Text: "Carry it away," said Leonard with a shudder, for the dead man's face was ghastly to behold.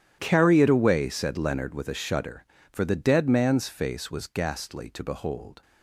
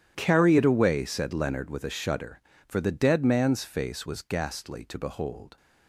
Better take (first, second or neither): neither